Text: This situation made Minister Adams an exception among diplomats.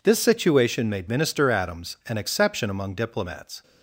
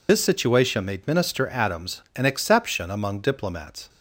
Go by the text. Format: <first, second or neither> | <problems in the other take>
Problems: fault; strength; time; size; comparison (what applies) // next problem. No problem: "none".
first | loses the start of "This"; at 0.0 s; 100 ms